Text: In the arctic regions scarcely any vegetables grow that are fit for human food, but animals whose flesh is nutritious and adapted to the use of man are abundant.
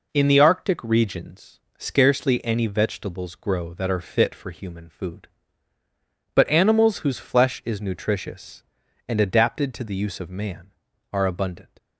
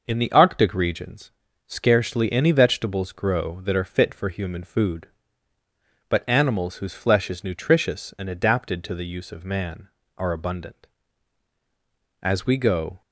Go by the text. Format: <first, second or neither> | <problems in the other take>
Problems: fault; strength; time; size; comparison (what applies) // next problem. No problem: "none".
first | pauses between "regions" and "scarcely"; slight; at 1.3 s; 0.36 s long; slight in the first // goes on to say "As we go"; noticeable; from 12.2 s on; 0.80 s long